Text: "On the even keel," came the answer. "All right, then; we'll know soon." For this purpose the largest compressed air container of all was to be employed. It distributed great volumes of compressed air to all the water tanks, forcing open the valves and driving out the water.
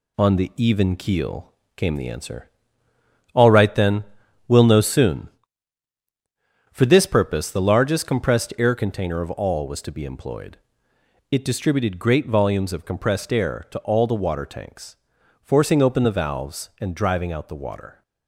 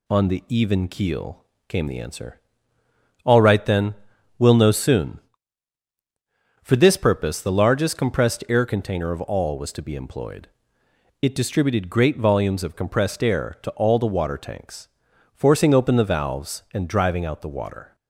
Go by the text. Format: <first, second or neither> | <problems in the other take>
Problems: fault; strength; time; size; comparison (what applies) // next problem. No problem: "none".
second | gets quieter; noticeable; throughout; 4.5 dB